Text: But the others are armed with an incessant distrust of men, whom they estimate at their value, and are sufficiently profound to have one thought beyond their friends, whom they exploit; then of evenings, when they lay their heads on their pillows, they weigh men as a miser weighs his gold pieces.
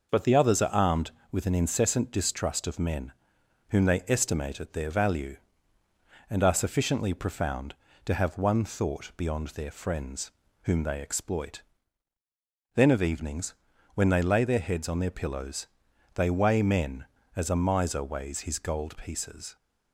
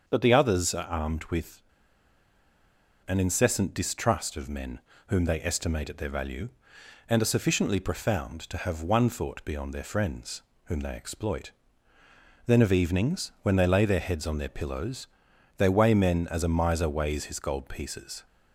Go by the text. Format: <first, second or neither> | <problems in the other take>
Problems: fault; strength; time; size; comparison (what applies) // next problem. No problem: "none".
first | starts louder than the rest; until 1.0 s; 6.5 dB // pauses between "with" and "an"; strong; at 1.6 s; 1.4 s long